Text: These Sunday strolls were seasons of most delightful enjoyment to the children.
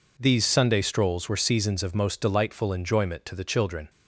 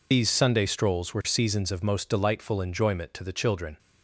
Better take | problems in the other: first | loses the start of "These"; at 0.1 s; 75 ms

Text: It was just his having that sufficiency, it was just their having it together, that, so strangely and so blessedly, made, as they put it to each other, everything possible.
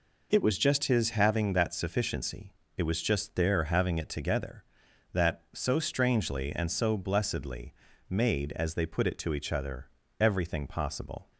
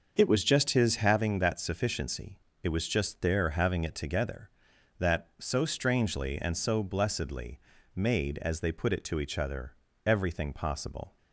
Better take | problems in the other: first | starts louder than the rest; until 1.2 s; 6.5 dB

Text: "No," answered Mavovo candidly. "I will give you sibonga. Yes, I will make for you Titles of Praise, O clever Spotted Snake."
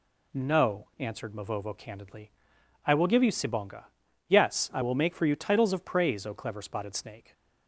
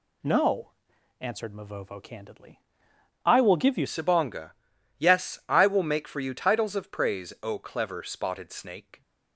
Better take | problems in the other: first | changes voice at "sibonga"; from 3.8 s on; 5.2 s long

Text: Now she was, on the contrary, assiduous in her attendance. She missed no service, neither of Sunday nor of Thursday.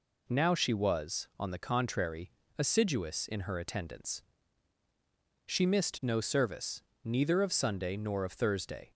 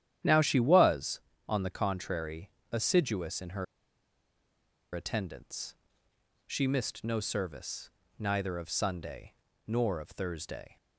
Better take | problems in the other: first | starts louder than the rest; strong; until 1.5 s; 10.5 dB // pauses between "her" and "attendance"; strong; at 3.6 s; 1.2 s long // pauses between "Sunday" and "nor"; slight; at 9.3 s; 0.34 s long

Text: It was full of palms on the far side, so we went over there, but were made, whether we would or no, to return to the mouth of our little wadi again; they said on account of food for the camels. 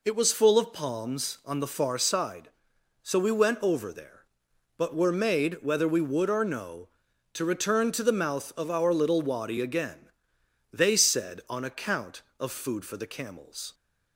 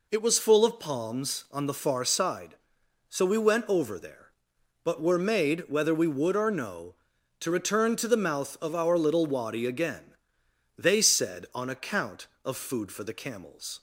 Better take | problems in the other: neither | none

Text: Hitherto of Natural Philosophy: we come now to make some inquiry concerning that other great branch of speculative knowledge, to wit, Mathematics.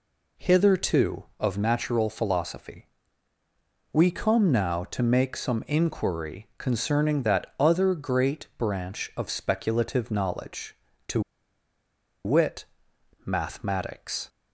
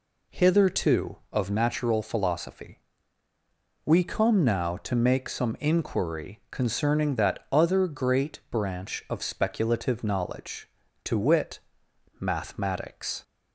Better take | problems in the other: second | pauses between "to" and "wit"; at 11.2 s; 1.0 s long

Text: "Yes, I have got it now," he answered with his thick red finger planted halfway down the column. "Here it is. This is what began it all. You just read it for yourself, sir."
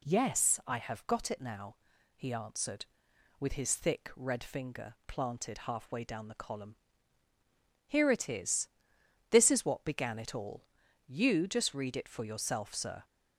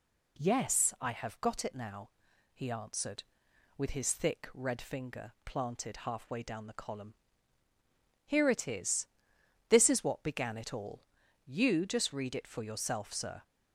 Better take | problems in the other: neither | none

